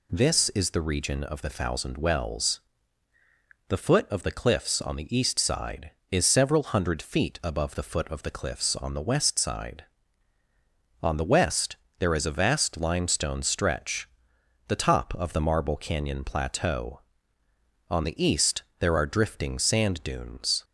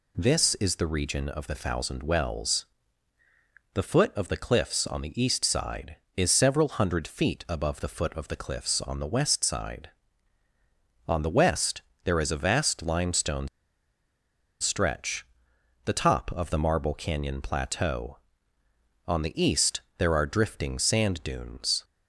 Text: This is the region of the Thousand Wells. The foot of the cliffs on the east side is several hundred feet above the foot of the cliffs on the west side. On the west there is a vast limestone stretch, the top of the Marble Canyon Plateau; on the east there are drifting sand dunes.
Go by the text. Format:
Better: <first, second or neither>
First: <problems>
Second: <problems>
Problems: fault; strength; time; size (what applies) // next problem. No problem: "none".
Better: first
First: pauses between "west" and "there"; slight; at 11.7 s; 0.24 s long // pauses between "east" and "there"; slight; at 18.6 s; 0.16 s long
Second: pauses between "west" and "there"; slight; at 11.8 s; 0.24 s long // pauses between "limestone" and "stretch"; at 13.4 s; 1.1 s long // pauses between "east" and "there"; slight; at 19.8 s; 0.16 s long